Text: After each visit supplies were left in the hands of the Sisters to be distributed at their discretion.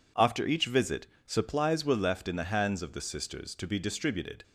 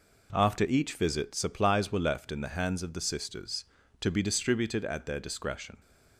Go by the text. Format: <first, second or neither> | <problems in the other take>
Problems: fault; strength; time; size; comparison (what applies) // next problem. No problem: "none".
second | pauses between "visit" and "supplies"; slight; at 1.0 s; 0.18 s long // stops before "at their discretion"; at 4.4 s